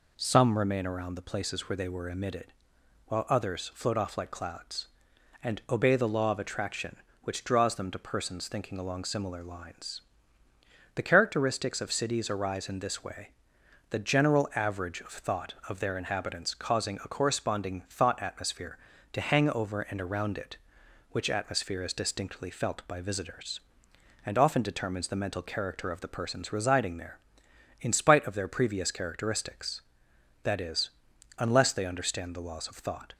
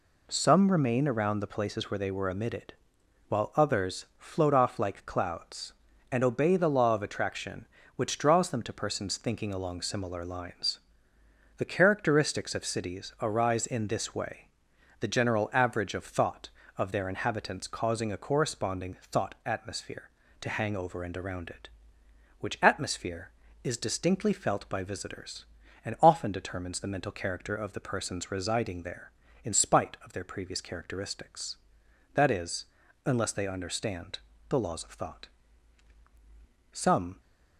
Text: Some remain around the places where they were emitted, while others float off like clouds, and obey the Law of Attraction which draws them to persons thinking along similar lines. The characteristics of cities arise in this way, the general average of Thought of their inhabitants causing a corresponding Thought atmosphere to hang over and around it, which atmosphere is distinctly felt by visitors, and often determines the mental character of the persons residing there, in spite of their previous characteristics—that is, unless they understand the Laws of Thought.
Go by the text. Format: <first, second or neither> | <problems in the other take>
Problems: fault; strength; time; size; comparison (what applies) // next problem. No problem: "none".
first | pauses between "corresponding" and "Thought"; slight; at 18.9 s; 0.16 s long // pauses between "understand" and "the"; slight; at 34.1 s; 0.30 s long // goes on to say "Some"; slight; from 36.7 s on; 0.48 s long